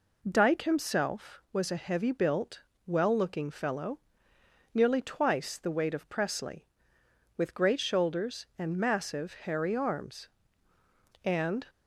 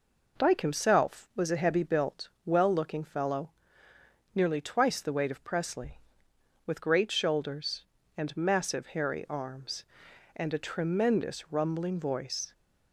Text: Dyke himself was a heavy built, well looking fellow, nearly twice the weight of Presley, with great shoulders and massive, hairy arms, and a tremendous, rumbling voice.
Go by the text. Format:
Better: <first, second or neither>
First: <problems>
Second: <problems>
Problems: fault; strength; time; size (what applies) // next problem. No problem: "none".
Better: second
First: stops before "a tremendous rumbling voice"; at 11.6 s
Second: none